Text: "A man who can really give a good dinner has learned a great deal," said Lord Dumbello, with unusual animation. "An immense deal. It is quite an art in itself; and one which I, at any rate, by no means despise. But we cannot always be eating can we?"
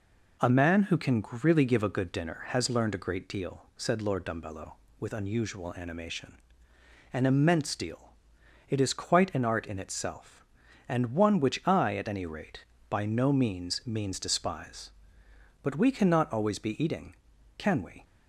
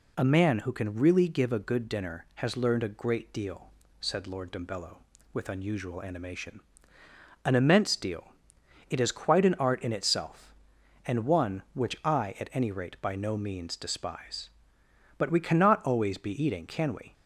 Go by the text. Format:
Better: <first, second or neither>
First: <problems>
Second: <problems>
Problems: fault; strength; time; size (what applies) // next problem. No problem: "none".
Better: second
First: pauses between "can" and "really"; slight; at 1.2 s; 0.18 s long // says "means" twice; at 13.8 s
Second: none